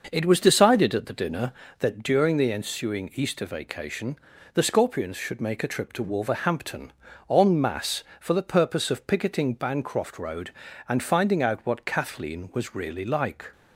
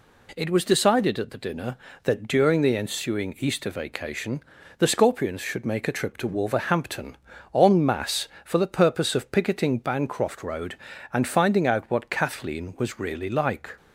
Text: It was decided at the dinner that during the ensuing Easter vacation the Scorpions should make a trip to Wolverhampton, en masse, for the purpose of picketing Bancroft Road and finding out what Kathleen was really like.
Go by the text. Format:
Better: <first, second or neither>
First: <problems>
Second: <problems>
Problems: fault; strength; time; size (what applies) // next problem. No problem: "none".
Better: second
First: starts louder than the rest; noticeable; until 1.6 s; 6 dB // pauses between "vacation" and "the"; slight; at 4.1 s; 0.36 s long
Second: pauses between "vacation" and "the"; slight; at 4.4 s; 0.36 s long